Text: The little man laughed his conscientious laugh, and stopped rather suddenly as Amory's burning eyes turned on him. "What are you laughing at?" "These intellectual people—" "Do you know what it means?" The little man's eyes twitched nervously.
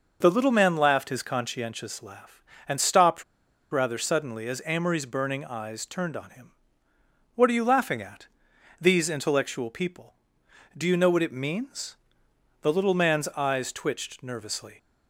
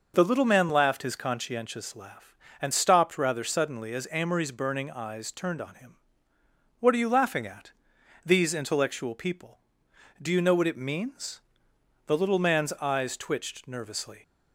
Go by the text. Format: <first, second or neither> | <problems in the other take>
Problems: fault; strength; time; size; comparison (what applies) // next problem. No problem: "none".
second | pauses between "stopped" and "rather"; noticeable; at 3.2 s; 0.48 s long